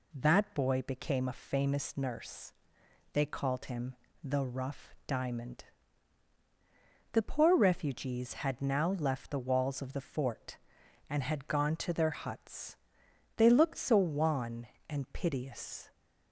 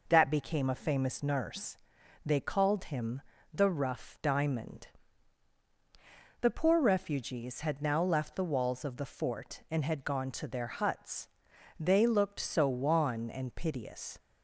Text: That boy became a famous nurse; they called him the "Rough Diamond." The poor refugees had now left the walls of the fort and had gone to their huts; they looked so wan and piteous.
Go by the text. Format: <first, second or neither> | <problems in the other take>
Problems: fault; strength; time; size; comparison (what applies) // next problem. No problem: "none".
first | skips "boy"; at 0.3 s // pauses between "him" and "the"; slight; at 3.2 s; 0.32 s long; slight in the first